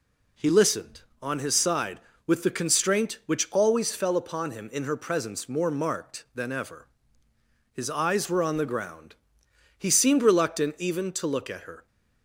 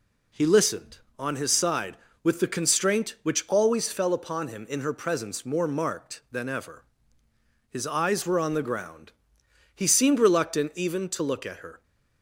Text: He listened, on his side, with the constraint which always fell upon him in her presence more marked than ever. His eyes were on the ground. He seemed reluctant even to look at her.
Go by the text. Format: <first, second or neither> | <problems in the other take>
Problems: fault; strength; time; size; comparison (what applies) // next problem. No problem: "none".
neither | none